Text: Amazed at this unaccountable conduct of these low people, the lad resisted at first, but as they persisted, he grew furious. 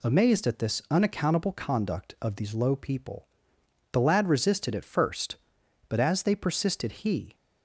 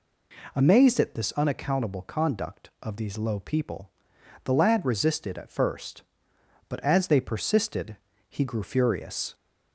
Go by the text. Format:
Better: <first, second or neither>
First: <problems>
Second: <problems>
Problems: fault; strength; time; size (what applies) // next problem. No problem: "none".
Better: second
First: stops before "grew furious"; at 7.3 s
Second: none